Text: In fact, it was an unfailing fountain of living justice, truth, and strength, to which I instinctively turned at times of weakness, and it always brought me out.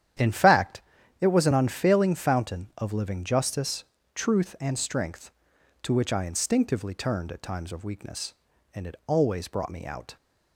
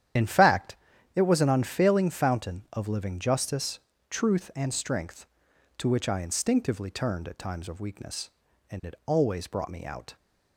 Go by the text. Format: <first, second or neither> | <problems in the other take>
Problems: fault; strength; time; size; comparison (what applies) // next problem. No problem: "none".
first | loses the start of "In"; at 0.1 s; 40 ms // starts louder than the rest; strong; until 1.5 s; 10 dB; strong in the first